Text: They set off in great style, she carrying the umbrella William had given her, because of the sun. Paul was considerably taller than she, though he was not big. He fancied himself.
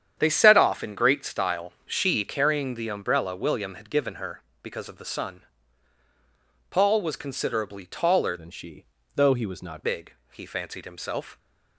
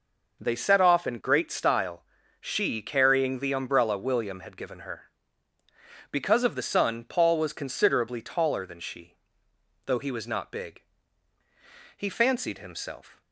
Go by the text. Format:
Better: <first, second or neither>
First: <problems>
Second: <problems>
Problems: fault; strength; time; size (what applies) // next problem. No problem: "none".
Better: second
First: starts louder than the rest; strong; until 1.1 s; 8.5 dB // changes voice from "than" to "not"; from 8.3 to 9.8 s; 1.5 s long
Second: none